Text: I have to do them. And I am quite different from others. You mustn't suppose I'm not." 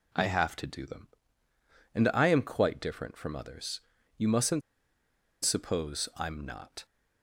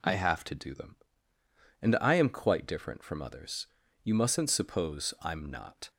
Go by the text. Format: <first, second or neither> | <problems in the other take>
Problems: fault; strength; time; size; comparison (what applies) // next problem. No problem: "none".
second | pauses between "mustn't" and "suppose"; noticeable; at 4.6 s; 0.84 s long